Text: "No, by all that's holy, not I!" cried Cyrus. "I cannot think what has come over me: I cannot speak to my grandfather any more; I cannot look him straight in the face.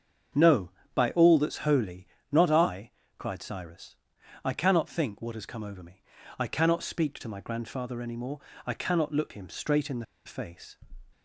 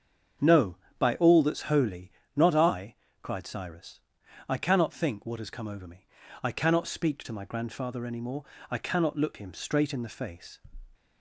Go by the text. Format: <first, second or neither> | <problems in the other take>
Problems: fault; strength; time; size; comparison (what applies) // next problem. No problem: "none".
second | starts louder than the rest; strong; until 1.5 s; 7 dB; strong in the second // pauses between "the" and "face"; slight; at 10.0 s; 0.21 s long